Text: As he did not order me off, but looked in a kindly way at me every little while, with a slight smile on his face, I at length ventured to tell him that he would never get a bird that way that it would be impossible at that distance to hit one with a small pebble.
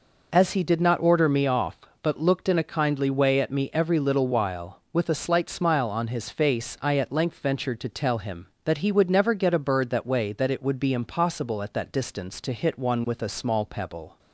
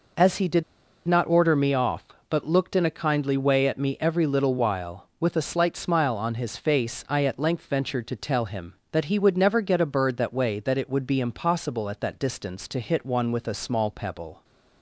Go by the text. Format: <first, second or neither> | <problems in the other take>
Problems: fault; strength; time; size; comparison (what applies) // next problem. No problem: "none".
first | pauses between "did" and "not"; at 0.6 s; 0.44 s long